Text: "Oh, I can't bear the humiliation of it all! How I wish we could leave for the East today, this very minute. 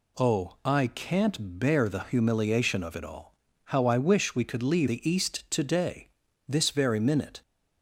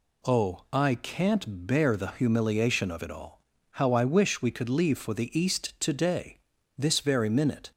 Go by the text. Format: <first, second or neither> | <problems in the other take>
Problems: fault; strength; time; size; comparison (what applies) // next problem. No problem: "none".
second | skips "for"; at 4.8 s